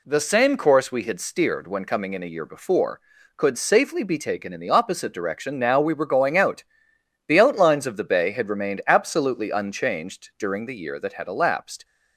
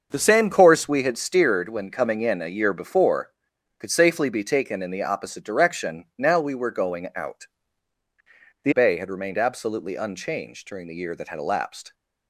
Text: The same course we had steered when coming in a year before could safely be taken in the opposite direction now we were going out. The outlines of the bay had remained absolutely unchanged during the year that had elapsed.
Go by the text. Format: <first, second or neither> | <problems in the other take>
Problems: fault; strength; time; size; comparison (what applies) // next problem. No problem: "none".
first | starts louder than the rest; until 1.1 s; 6.5 dB // skips "outlines of the"; at 8.7 s